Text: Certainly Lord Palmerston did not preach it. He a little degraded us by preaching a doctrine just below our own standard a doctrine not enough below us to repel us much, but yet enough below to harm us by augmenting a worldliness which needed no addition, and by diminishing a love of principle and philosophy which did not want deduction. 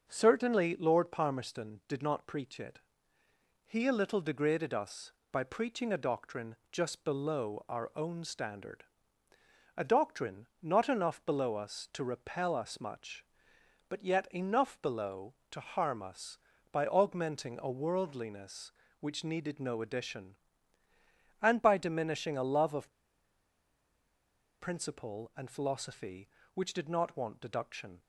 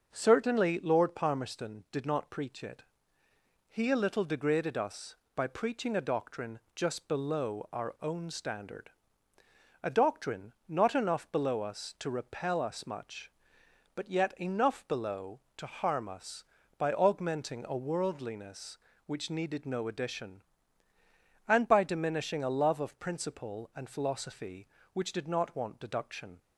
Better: second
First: starts louder than the rest; until 1.0 s; 6.5 dB // pauses between "doctrine" and "just"; slight; at 6.5 s; 0.16 s long // pauses between "standard" and "a"; noticeable; at 8.8 s; 0.92 s long // pauses between "of" and "principle"; strong; at 22.9 s; 1.6 s long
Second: starts louder than the rest; until 1.1 s; 6.5 dB // pauses between "doctrine" and "just"; slight; at 6.5 s; 0.16 s long // pauses between "standard" and "a"; noticeable; at 8.8 s; 0.92 s long

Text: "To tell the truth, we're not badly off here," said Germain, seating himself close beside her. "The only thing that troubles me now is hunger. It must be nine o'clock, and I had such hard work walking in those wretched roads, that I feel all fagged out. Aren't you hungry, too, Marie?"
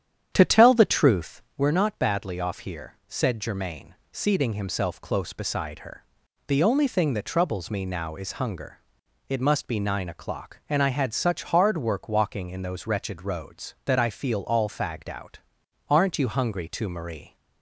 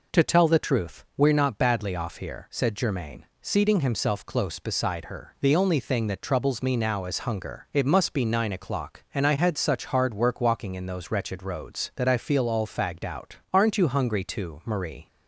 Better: second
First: starts louder than the rest; strong; until 1.5 s; 9.5 dB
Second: none

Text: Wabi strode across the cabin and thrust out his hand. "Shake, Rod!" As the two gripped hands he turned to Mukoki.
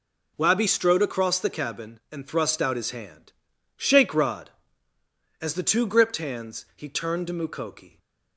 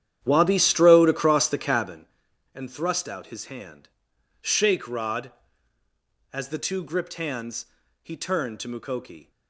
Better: first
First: none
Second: starts louder than the rest; strong; until 2.1 s; 10 dB // pauses between "hands" and "he"; slight; at 7.6 s; 0.36 s long

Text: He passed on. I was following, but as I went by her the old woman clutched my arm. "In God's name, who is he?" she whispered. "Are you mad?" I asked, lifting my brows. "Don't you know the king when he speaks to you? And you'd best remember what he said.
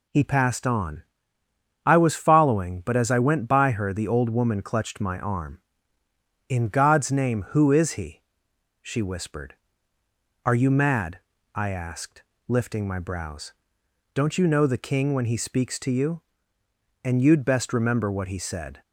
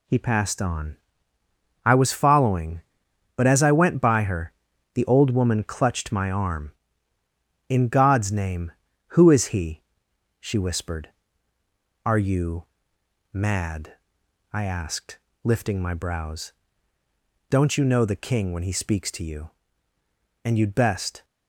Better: first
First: none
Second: pauses between "her" and "the"; at 4.5 s; 0.42 s long // pauses between "you" and "mad"; noticeable; at 12.6 s; 0.68 s long // stops before "remember what he said"; at 21.2 s

